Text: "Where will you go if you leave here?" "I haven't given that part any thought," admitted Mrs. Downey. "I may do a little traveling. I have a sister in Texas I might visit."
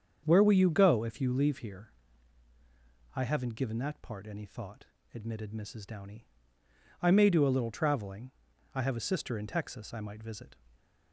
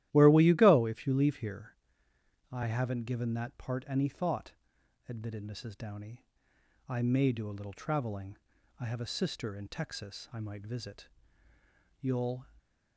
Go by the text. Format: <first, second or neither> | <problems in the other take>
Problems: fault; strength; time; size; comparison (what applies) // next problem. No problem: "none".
first | starts louder than the rest; strong; until 1.1 s; 13.5 dB; strong in the first // goes on to say "You'll"; slight; from 11.9 s on; 0.44 s long